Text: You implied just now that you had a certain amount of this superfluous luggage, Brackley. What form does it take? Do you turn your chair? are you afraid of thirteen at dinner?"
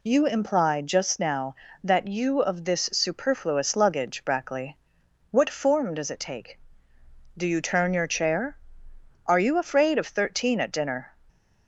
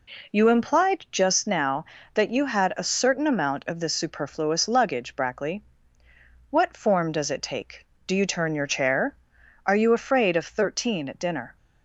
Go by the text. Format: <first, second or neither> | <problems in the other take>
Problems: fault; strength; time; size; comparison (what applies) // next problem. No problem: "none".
second | skips "had a certain amount"; at 2.4 s